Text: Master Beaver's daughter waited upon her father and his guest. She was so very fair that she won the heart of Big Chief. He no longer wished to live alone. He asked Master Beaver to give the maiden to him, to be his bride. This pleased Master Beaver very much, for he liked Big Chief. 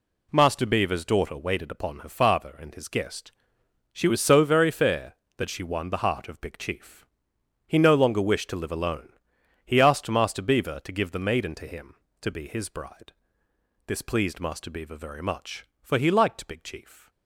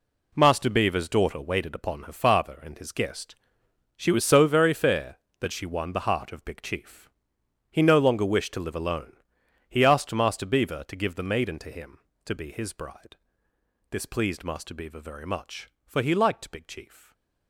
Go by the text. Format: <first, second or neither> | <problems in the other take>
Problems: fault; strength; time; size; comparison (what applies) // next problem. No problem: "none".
first | gets quieter; strong; throughout; 11 dB // stays silent after the last word; slight; from 16.9 s on; 0.5 s long